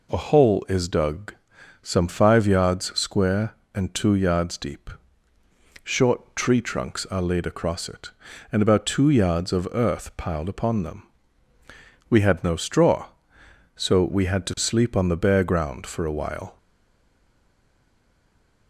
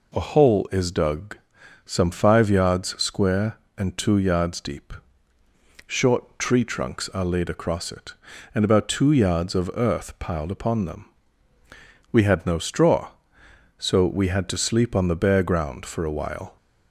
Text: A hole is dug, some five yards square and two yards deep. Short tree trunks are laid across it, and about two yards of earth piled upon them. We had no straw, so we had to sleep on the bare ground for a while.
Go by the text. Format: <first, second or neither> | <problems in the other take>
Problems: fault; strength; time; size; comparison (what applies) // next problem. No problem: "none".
second | stays silent after the last word; from 16.5 s on; 2.1 s long